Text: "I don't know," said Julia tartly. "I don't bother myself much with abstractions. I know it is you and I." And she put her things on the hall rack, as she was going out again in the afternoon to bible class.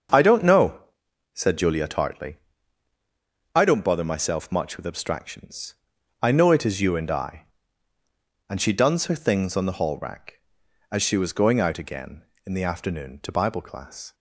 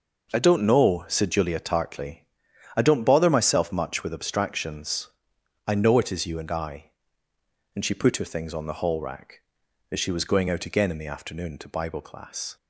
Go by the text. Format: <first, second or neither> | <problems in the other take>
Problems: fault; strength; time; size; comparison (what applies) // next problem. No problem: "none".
second | starts louder than the rest; until 1.5 s; 7 dB // says "duns" for "put"; at 8.7 s